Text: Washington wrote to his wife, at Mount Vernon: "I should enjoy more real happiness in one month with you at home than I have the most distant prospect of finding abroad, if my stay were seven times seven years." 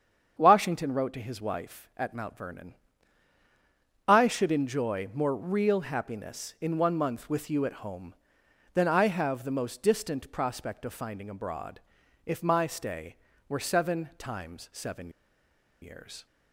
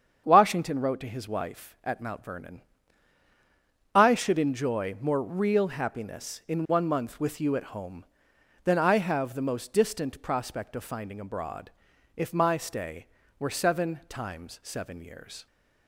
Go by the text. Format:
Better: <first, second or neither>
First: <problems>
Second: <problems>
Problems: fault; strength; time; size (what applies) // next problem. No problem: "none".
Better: second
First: starts louder than the rest; strong; until 1.3 s; 7.5 dB // pauses between "seven" and "years"; noticeable; at 15.0 s; 0.72 s long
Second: starts louder than the rest; strong; until 1.2 s; 7.5 dB